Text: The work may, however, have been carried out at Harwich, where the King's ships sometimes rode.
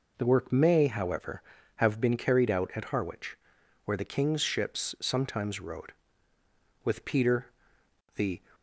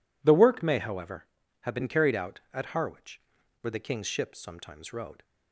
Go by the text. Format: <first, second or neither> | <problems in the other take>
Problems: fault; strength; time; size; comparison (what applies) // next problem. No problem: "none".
second | goes on to say "With Peter the"; from 6.8 s on; 1.5 s long